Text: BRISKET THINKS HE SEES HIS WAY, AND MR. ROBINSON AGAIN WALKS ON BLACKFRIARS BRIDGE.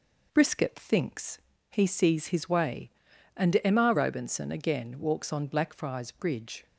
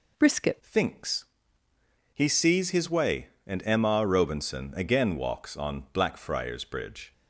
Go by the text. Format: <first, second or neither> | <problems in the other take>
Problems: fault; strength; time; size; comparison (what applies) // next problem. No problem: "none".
first | changes voice at "THINKS"; from 0.6 s on; 6.5 s long // pauses between "THINKS" and "HE"; noticeable; at 1.2 s; 0.88 s long; slight in the first